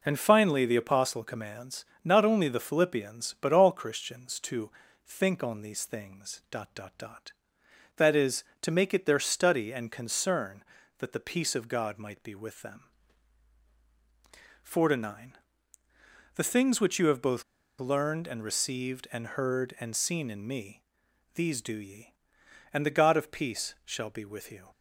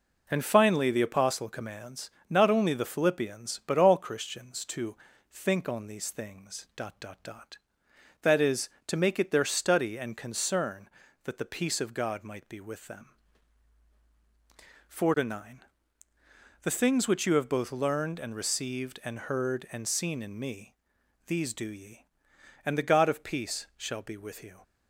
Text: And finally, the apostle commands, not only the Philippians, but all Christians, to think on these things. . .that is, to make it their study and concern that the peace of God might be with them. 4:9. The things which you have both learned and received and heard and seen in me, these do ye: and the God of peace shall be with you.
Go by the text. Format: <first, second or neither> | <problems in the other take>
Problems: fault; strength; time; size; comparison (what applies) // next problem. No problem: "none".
second | pauses between "to" and "think"; slight; at 4.6 s; 0.36 s long; slight in the second // pauses between "both" and "learned"; slight; at 17.4 s; 0.35 s long